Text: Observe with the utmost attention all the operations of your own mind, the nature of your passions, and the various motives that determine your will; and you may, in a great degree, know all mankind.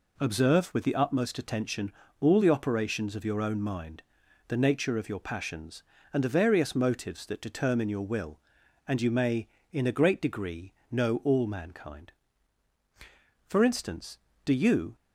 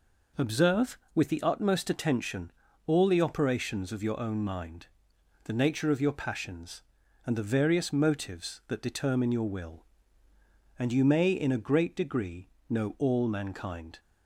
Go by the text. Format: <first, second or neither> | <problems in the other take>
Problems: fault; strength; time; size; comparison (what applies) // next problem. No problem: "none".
second | pauses between "attention" and "all"; slight; at 1.9 s; 0.30 s long; slight in the second // goes on to say "For instance do you"; from 13.4 s on; 1.4 s long